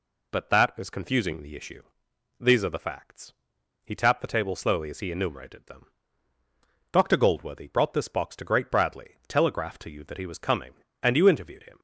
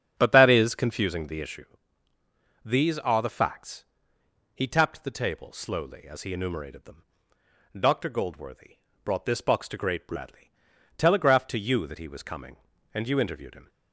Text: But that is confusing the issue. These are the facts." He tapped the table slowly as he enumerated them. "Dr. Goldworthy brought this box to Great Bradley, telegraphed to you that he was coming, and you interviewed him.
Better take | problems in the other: first | starts louder than the rest; strong; until 1.1 s; 8 dB // pauses between "Goldworthy" and "brought"; slight; at 8.7 s; 0.28 s long

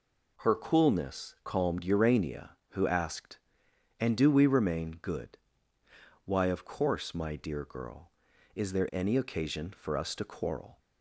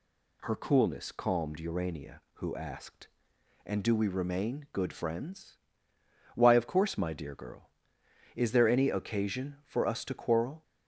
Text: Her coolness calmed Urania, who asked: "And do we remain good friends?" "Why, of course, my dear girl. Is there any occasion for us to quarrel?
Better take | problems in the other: second | skips "friends"; at 5.8 s

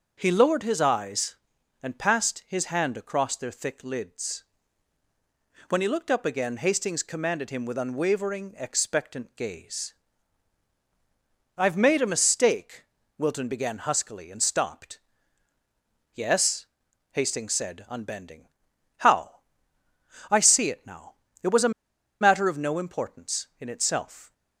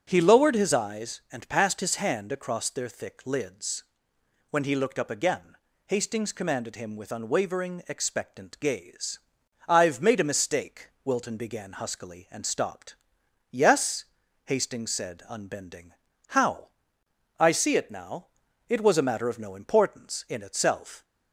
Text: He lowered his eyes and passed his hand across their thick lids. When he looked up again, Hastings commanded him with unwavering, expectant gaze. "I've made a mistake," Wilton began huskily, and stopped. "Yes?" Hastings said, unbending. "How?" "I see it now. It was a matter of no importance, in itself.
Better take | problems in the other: second | starts louder than the rest; until 1.1 s; 6.5 dB; also in the second // pauses between "a" and "matter"; noticeable; at 21.7 s; 0.49 s long

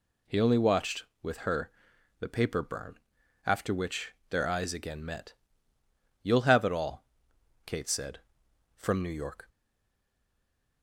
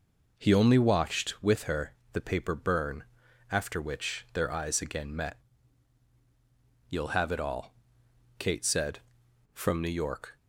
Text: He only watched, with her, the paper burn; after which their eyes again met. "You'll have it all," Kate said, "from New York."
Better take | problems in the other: second | pauses between "which" and "their"; slight; at 4.1 s; 0.18 s long // stays silent after the last word; noticeable; from 9.4 s on; 1.4 s long

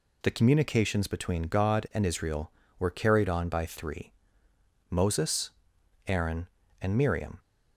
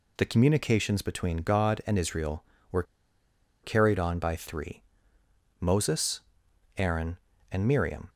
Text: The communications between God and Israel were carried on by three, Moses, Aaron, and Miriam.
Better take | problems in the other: first | pauses between "were" and "carried"; noticeable; at 2.8 s; 0.79 s long

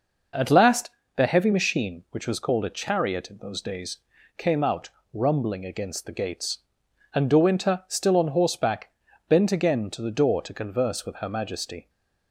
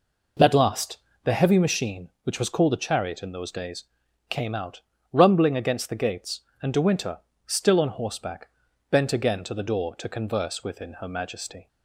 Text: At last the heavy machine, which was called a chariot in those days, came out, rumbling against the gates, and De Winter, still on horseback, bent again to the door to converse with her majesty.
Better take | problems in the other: first | pauses between "last" and "the"; slight; at 0.9 s; 0.26 s long; slight in the first // says "within" for "with"; at 10.6 s

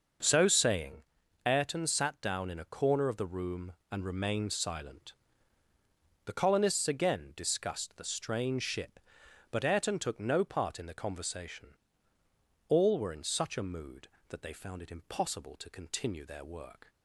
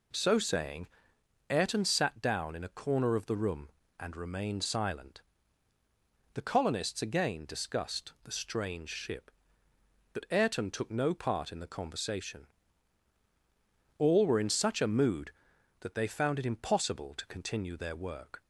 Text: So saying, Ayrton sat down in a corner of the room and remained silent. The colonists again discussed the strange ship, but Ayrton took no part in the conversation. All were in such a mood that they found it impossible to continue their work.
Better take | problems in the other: neither | none

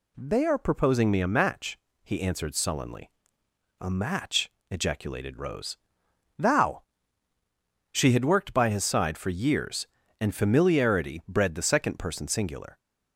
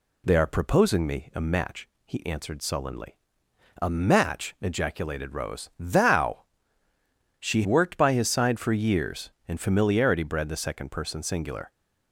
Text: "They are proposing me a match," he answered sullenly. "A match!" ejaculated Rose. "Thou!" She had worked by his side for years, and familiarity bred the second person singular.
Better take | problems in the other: first | skips "had"; at 7.6 s

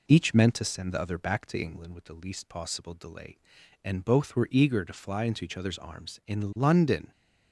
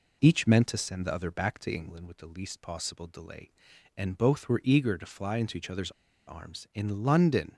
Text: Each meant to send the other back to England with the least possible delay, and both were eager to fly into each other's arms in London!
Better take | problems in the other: first | pauses between "other's" and "arms"; at 5.9 s; 0.36 s long

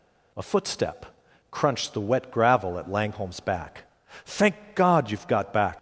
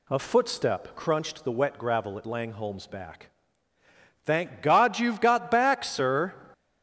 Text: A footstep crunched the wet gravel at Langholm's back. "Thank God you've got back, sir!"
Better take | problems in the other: second | pauses between "footstep" and "crunched"; noticeable; at 1.0 s; 0.46 s long // stops before "sir"; at 5.7 s

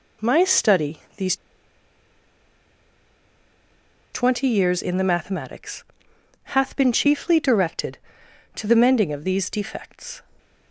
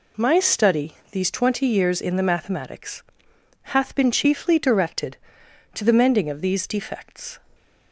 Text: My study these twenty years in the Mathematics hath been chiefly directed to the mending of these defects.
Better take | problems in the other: second | pauses between "these" and "twenty"; strong; at 1.3 s; 2.7 s long // pauses between "Mathematics" and "hath"; noticeable; at 5.8 s; 0.60 s long; noticeable in the second

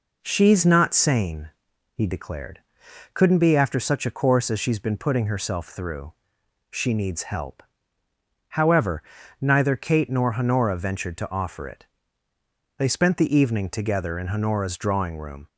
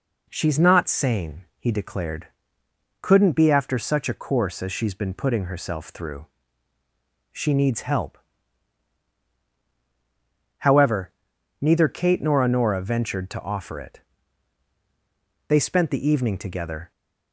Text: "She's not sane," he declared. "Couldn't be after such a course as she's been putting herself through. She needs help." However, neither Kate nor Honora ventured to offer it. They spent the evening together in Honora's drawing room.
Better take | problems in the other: first | stops before "in Honora's drawing room"; at 16.9 s

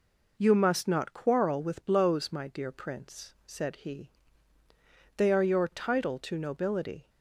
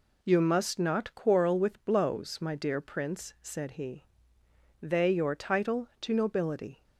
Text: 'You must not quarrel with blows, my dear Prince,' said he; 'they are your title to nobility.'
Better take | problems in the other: first | skips "are"; at 5.1 s

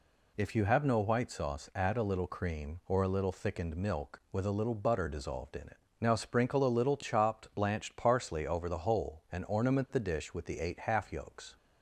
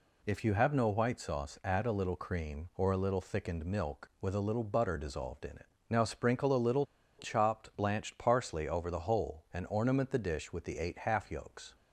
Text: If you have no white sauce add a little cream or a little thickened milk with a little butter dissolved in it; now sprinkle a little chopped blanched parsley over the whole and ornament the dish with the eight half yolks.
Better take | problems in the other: first | pauses between "little" and "chopped"; slight; at 6.8 s; 0.33 s long

